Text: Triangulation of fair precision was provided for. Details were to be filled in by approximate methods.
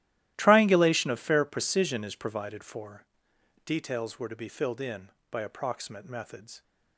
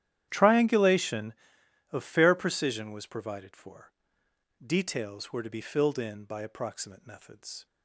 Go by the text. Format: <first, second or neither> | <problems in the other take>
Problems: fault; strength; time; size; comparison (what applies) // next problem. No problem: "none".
second | starts louder than the rest; strong; until 1.3 s; 14 dB; strong in the second // says "is" for "was"; at 2.0 s